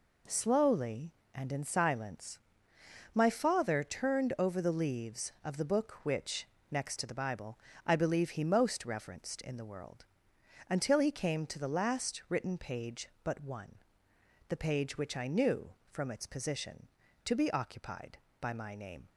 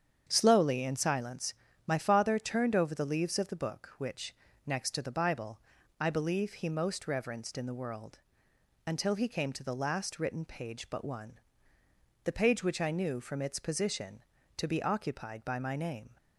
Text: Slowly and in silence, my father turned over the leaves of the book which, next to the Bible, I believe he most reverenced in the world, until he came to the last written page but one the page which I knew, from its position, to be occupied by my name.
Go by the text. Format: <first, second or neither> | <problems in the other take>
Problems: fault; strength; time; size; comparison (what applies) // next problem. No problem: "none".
first | starts louder than the rest; strong; until 1.2 s; 8 dB // skips "and"; at 0.8 s // pauses between "one" and "the"; noticeable; at 11.3 s; 0.86 s long; noticeable in the first